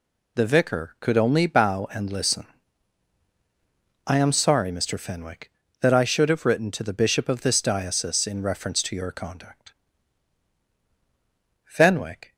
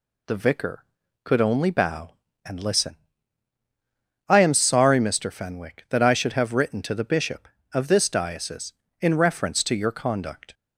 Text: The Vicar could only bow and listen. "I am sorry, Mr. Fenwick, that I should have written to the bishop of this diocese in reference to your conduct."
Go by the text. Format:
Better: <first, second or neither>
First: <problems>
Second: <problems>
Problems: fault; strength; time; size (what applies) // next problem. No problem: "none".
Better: second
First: goes on to say "Fenwick"; noticeable; from 11.6 s on; 0.70 s long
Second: none